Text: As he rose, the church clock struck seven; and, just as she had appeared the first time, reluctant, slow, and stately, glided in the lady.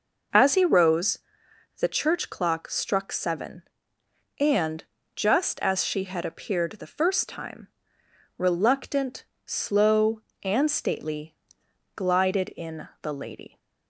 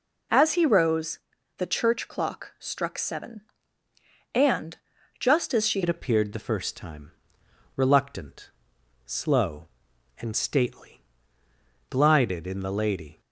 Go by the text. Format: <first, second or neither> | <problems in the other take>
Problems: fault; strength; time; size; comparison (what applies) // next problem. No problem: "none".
first | changes voice at "had"; from 5.8 s on; 7.3 s long